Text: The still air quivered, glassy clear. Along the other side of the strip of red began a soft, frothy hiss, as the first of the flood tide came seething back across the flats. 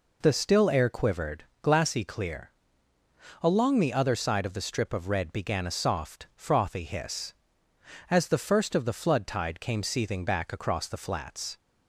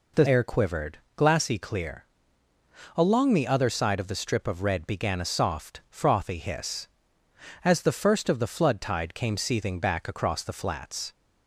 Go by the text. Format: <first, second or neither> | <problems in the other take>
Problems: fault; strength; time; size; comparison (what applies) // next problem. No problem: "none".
first | skips "still"; at 0.2 s